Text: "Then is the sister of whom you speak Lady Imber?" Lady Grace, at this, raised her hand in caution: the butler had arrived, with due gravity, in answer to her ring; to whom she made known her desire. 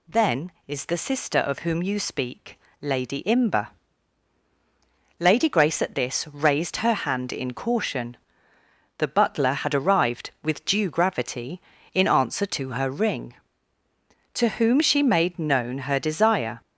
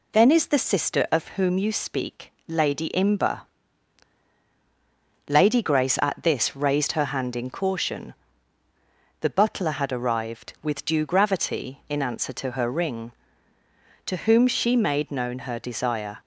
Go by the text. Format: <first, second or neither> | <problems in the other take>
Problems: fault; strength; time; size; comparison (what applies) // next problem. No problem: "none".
neither | pauses between "speak" and "Lady"; slight; the same in both